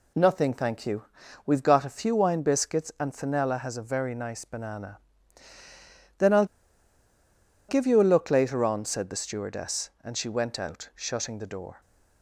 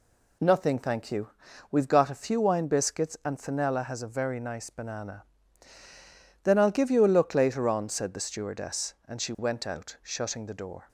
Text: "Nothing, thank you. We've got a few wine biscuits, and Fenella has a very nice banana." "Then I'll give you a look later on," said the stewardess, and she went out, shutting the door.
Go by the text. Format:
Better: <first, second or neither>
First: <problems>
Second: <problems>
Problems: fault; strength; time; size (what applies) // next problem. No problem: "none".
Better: second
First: pauses between "I'll" and "give"; at 6.4 s; 1.2 s long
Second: none